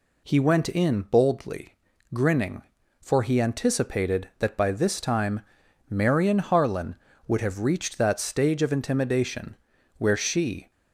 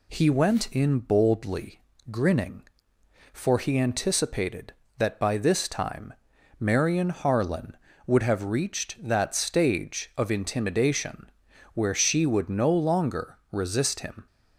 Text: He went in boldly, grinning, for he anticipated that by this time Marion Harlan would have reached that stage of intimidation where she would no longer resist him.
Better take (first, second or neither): second